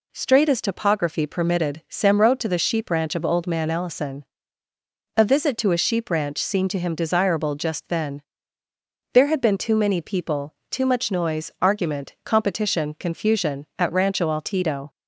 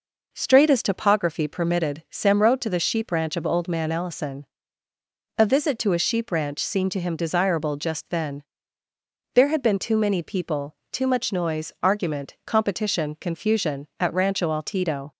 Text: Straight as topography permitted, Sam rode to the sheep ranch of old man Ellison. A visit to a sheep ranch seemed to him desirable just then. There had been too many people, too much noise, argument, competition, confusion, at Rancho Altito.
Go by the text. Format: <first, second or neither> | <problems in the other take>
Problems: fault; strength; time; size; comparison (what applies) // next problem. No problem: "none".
first | starts louder than the rest; noticeable; until 1.3 s; 5 dB